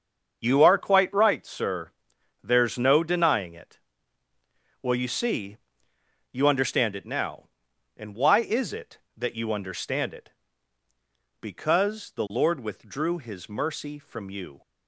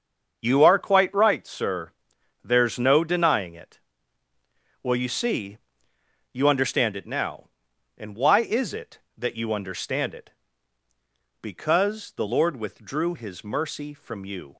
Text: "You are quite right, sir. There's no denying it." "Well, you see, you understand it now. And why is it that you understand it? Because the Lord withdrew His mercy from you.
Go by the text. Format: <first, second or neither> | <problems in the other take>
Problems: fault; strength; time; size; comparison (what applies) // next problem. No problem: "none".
neither | starts louder than the rest; the same in both